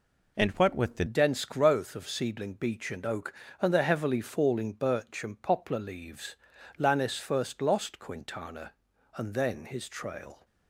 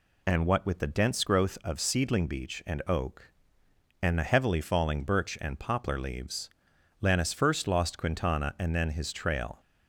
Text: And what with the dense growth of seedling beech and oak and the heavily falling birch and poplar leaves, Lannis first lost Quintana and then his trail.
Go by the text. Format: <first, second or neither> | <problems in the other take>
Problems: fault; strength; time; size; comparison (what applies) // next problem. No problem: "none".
second | changes voice at "dense"; from 1.0 s on; 9.4 s long